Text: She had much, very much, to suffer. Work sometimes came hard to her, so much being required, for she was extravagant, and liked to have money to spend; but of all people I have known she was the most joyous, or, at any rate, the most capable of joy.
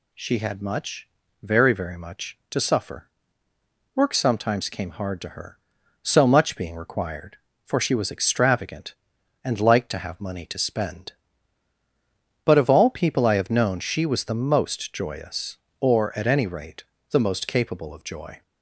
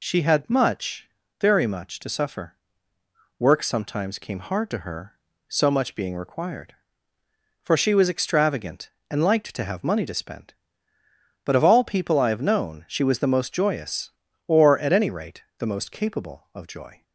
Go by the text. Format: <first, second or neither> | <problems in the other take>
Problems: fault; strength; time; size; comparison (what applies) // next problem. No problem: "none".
second | says "very" twice; at 1.7 s